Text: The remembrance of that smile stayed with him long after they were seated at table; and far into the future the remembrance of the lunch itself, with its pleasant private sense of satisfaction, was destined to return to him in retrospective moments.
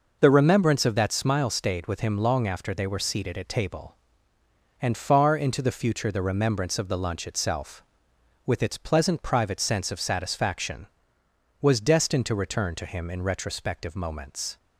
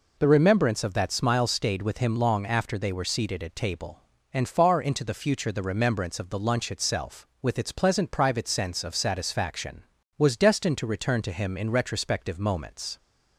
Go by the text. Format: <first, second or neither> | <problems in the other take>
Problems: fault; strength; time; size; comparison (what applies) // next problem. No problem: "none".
neither | none